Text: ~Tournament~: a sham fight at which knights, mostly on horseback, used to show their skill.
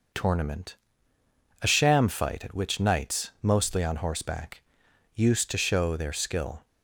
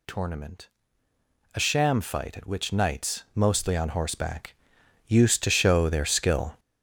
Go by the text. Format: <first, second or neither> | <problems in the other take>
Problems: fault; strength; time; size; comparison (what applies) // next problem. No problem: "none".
first | gets louder; strong; throughout; 9 dB